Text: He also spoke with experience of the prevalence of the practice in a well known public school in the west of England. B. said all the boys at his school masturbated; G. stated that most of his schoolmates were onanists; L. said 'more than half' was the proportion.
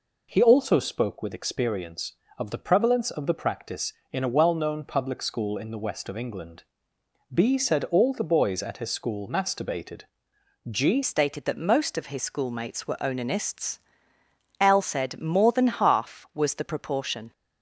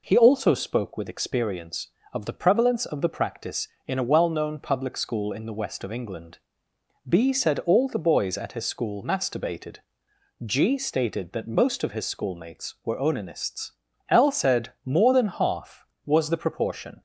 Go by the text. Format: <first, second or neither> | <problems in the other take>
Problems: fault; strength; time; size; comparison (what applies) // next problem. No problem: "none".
second | changes voice at "stated"; from 11.0 s on; 6.3 s long